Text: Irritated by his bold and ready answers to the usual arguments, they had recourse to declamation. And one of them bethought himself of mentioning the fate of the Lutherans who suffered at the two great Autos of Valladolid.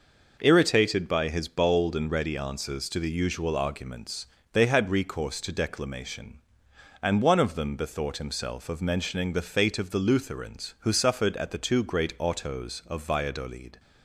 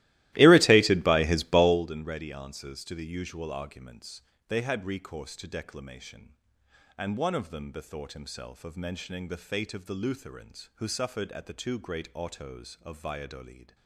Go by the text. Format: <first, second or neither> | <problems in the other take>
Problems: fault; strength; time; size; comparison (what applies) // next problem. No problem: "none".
first | starts louder than the rest; strong; until 1.9 s; 17 dB